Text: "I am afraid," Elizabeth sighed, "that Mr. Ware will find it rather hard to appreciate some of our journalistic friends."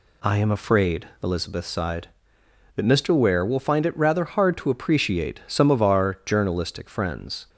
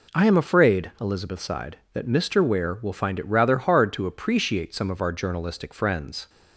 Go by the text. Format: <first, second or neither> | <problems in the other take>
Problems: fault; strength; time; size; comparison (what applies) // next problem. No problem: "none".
neither | none